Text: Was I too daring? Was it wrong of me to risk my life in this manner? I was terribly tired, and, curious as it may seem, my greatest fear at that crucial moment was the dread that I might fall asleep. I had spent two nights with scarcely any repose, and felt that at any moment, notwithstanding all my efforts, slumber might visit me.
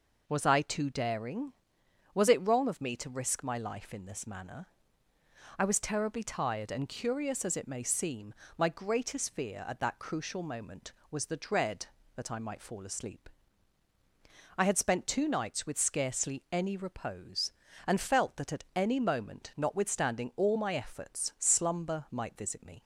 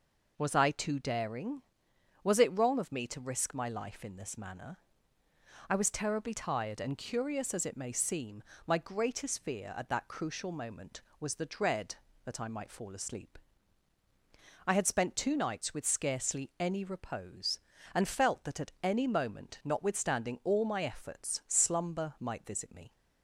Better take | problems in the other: neither | none

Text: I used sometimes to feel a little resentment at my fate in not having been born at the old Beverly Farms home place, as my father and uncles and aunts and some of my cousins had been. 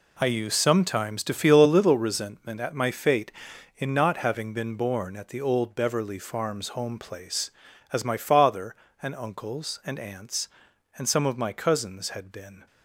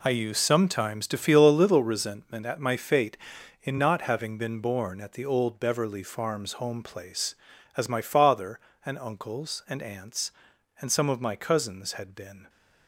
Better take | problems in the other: neither | none

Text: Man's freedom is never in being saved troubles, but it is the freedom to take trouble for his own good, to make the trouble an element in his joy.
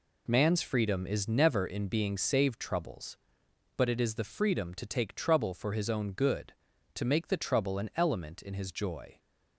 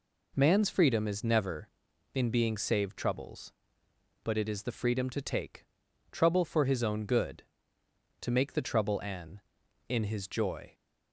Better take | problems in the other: first | pauses between "take" and "trouble"; noticeable; at 5.6 s; 0.46 s long // skips "element"; at 9.6 s

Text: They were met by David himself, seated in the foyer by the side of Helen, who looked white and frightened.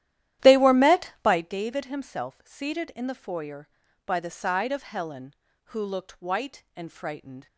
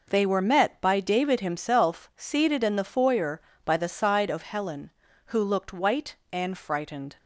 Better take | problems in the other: second | starts louder than the rest; strong; until 1.6 s; 12.5 dB

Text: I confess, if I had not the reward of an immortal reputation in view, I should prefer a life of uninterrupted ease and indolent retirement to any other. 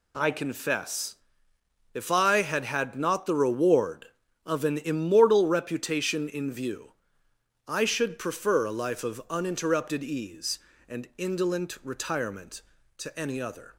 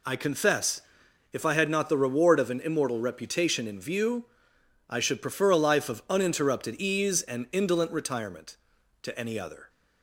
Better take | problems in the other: second | says "had" twice; at 2.6 s

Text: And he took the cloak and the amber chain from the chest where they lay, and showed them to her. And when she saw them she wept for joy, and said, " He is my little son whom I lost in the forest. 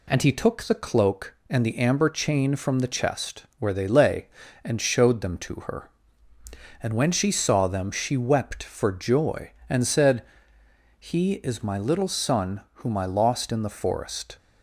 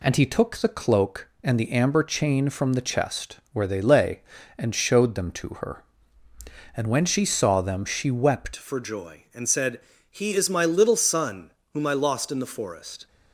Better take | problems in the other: first | changes voice at "for"; from 8.5 s on; 4.5 s long // pauses between "son" and "whom"; slight; at 11.5 s; 0.22 s long

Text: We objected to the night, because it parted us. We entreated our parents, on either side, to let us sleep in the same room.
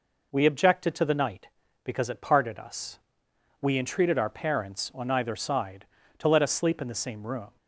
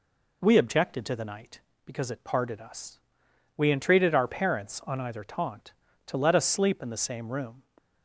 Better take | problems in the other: first | says "taunt" for "side"; at 5.2 s

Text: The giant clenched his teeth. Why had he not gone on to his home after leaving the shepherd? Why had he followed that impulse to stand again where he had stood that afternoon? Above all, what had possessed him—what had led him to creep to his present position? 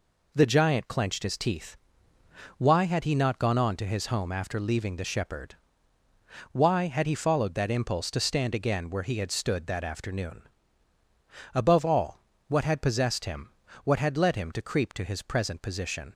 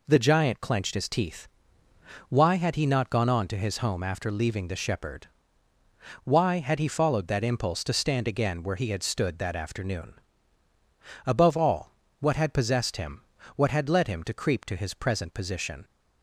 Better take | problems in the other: neither | none

